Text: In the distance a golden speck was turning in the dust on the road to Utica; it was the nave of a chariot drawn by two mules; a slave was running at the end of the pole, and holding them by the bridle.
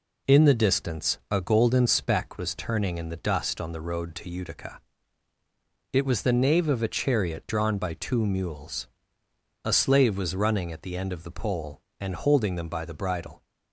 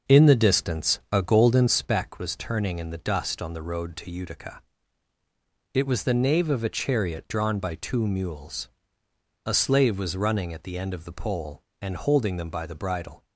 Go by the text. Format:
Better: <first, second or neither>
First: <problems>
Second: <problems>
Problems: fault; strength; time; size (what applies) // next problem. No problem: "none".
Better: first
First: none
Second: starts louder than the rest; until 1.8 s; 6.5 dB